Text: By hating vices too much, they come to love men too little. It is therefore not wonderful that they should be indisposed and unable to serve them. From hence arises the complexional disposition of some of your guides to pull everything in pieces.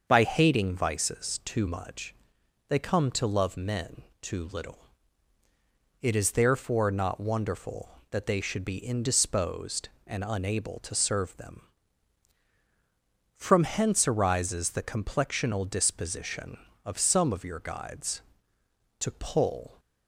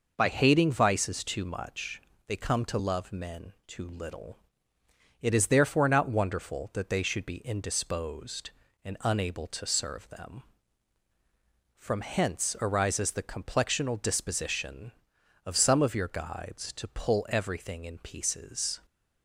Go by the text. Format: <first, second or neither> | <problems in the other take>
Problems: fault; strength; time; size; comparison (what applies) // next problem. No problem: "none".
second | starts louder than the rest; until 1.0 s; 6.5 dB // pauses between "men" and "too"; slight; at 4.0 s; 0.20 s long // stops before "everything in pieces"; at 19.7 s